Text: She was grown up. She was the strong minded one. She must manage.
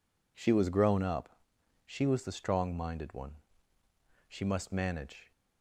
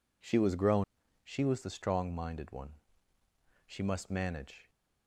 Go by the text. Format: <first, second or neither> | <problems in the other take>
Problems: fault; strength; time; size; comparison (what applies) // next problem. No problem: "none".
first | skips "up"; at 1.0 s